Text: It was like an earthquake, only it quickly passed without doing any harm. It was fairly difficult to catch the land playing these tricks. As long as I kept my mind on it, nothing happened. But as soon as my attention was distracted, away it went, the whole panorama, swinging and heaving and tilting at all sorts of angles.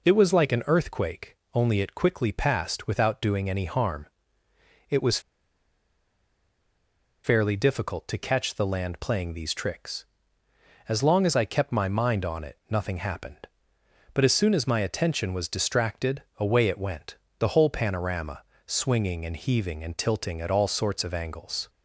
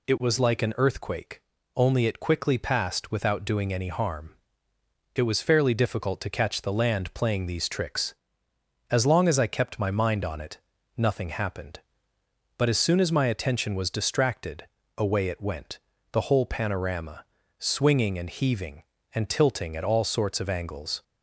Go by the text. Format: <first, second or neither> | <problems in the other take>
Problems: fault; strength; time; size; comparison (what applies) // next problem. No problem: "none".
second | pauses between "was" and "fairly"; strong; at 5.1 s; 2.0 s long